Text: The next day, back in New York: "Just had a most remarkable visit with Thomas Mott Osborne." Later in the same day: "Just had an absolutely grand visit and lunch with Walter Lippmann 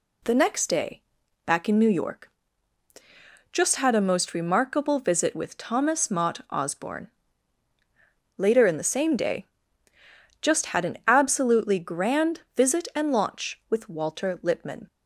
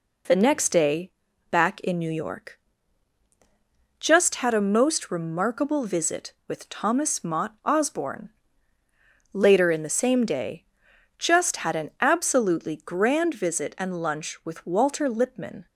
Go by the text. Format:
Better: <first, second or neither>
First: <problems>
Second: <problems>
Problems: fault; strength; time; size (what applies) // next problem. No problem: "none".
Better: second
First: says "launch" for "lunch"; at 13.1 s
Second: none